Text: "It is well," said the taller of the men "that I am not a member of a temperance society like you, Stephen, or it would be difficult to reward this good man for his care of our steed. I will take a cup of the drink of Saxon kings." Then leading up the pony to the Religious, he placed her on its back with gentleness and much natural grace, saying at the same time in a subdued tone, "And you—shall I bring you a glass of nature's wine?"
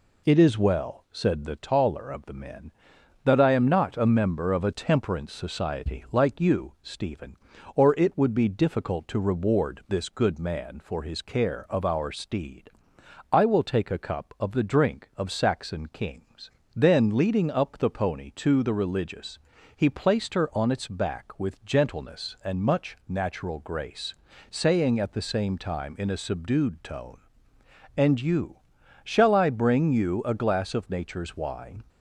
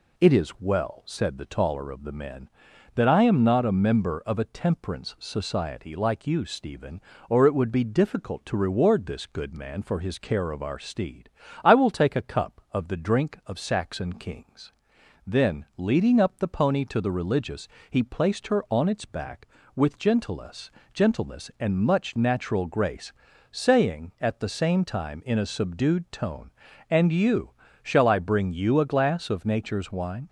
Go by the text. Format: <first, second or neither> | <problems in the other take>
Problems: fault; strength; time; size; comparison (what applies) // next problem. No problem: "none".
first | says "gentleness" twice; at 20.9 s